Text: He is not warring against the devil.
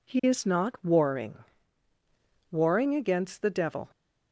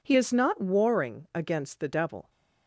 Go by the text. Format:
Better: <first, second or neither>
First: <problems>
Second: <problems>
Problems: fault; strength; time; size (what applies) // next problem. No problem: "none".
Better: second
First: says "warring" twice; at 2.5 s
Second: none